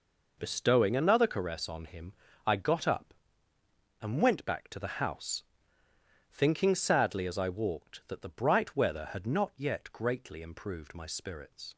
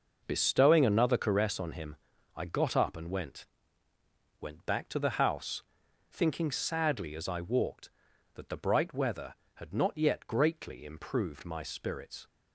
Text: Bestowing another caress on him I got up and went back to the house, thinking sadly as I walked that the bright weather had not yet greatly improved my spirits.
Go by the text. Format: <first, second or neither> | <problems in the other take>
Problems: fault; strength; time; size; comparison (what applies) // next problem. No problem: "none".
first | pauses between "him" and "I"; at 1.9 s; 0.38 s long; slight in the first // says "went" twice; at 4.3 s